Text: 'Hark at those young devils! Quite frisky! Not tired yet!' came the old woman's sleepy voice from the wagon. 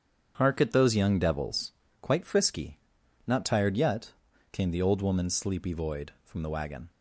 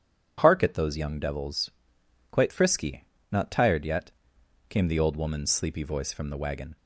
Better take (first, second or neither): second